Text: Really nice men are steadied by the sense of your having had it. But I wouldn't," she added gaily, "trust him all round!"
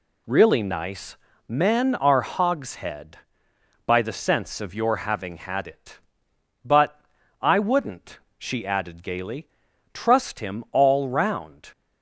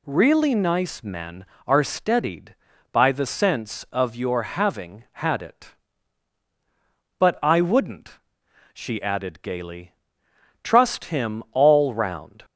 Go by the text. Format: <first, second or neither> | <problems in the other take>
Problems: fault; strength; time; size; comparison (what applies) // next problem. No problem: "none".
second | pauses between "nice" and "men"; slight; at 1.1 s; 0.32 s long // says "hogshead" for "steadied"; at 2.2 s // pauses between "But" and "I"; at 7.0 s; 0.40 s long